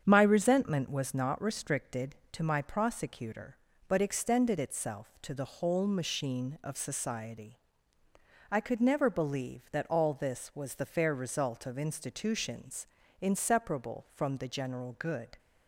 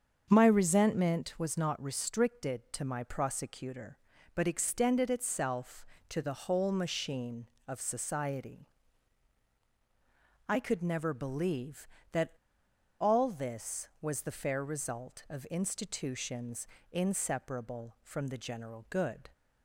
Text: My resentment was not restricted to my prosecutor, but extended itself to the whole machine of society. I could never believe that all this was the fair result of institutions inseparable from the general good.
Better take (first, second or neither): first